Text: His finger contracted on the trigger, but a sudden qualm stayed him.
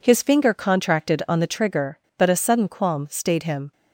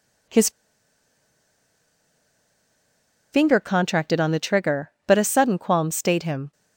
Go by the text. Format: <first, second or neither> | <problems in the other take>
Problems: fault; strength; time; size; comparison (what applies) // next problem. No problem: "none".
first | pauses between "His" and "finger"; strong; at 0.4 s; 2.8 s long